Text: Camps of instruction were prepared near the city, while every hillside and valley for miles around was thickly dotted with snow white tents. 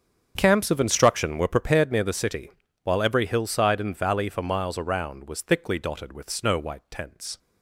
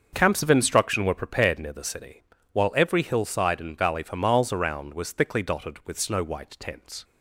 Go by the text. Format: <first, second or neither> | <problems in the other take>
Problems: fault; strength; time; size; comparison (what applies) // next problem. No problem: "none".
neither | starts louder than the rest; the same in both